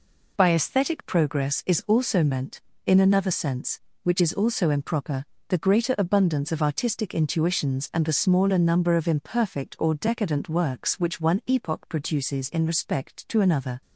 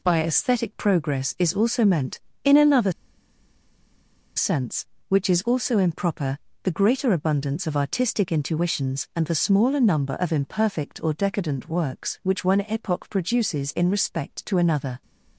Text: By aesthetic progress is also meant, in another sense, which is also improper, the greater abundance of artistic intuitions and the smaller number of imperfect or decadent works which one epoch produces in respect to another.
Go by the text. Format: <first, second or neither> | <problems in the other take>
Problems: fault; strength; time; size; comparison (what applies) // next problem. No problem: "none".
first | pauses between "another" and "sense"; strong; at 2.8 s; 1.4 s long